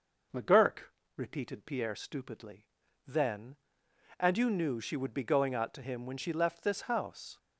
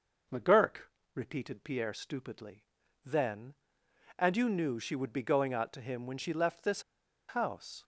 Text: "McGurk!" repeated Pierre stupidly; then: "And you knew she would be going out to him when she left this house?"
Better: first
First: none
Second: pauses between "this" and "house"; noticeable; at 6.8 s; 0.46 s long

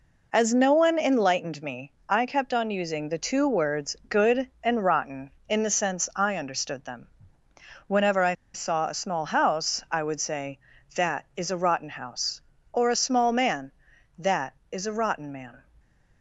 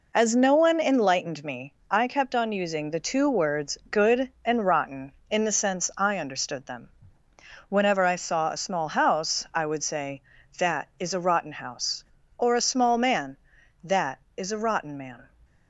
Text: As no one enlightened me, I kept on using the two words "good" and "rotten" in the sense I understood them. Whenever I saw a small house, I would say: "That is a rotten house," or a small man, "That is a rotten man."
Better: second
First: pauses between "I" and "saw"; slight; at 8.3 s; 0.19 s long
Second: none

